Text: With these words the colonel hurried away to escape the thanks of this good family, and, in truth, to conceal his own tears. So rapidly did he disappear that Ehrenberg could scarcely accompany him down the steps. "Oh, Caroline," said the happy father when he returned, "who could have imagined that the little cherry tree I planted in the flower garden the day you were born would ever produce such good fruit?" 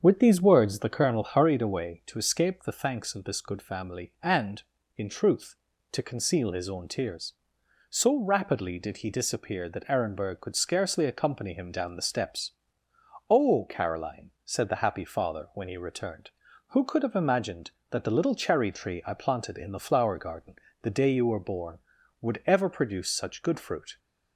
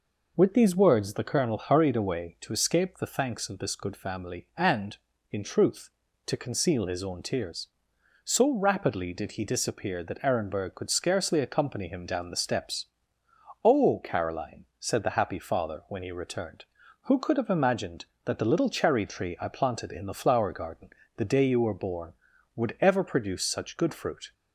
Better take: second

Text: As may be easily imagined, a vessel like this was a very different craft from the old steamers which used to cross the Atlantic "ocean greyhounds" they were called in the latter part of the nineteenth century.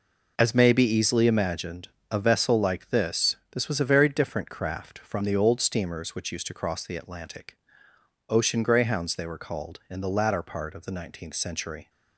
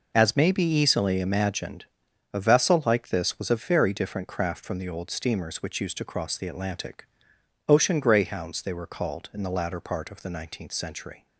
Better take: second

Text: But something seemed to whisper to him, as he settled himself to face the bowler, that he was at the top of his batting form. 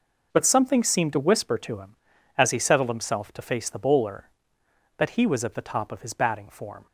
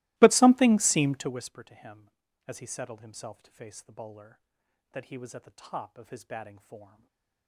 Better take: first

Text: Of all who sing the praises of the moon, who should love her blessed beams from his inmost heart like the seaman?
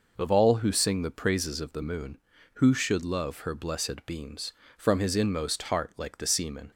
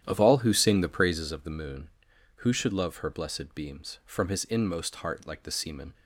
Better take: first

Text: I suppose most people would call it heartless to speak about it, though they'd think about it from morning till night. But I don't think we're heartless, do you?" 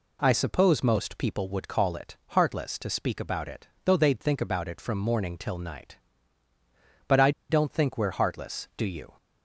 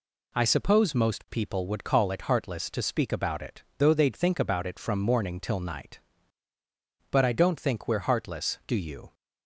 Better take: second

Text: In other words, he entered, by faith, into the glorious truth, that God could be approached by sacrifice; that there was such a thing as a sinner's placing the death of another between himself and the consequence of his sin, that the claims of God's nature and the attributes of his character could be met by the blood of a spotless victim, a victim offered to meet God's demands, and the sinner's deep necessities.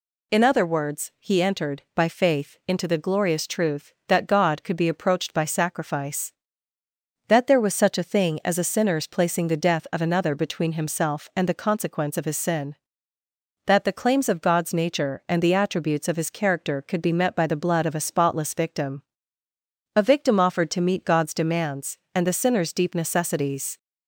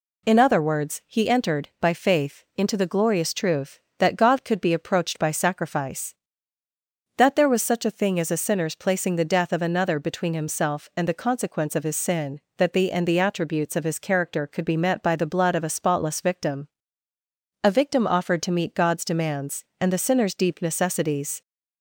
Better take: first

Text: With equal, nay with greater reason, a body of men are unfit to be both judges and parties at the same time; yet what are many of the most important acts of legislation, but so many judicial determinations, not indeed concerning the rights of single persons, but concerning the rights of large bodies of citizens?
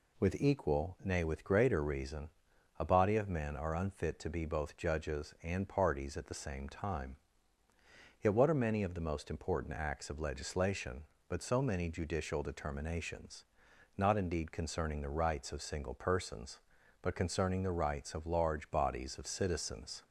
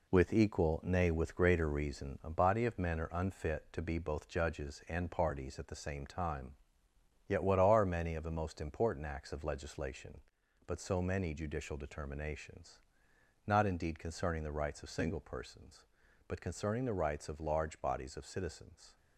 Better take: first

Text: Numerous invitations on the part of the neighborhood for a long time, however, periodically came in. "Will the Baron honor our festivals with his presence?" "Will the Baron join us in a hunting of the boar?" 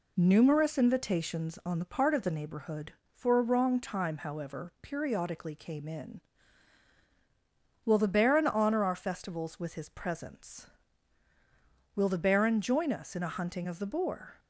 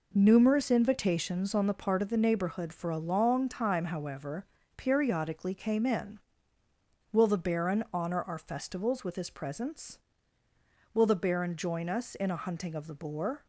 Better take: second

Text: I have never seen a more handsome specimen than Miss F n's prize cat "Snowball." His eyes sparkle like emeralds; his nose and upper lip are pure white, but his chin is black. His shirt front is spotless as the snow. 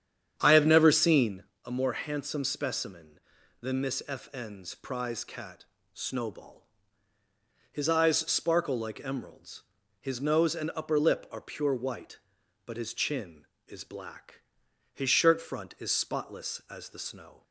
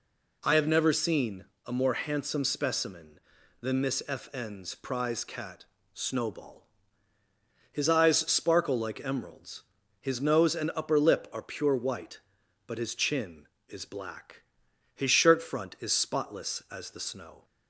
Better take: second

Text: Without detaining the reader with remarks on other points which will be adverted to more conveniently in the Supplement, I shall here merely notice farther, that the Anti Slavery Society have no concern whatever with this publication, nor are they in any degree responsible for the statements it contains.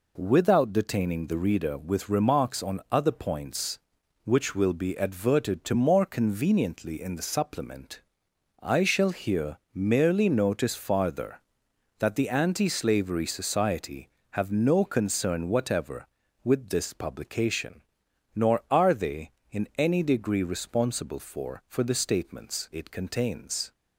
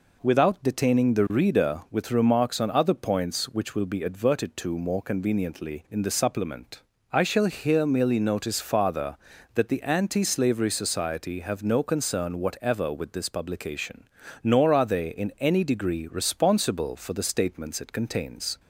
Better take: second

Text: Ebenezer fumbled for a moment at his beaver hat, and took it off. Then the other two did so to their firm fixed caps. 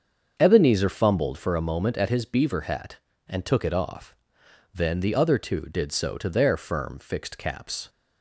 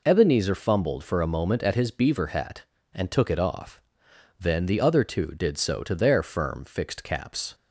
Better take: second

